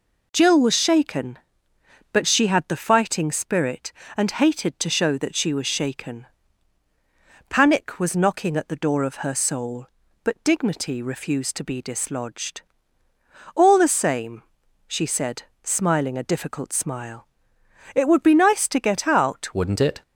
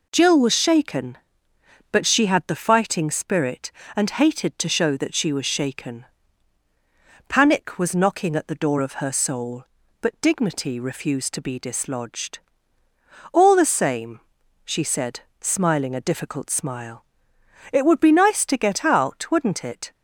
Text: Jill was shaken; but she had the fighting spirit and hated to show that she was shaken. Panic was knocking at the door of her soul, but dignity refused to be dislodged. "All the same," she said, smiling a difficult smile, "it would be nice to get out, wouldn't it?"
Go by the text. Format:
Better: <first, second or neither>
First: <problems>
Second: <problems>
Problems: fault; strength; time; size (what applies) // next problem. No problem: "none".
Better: second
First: changes voice at "wouldn't"; from 19.5 s on; 0.5 s long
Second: none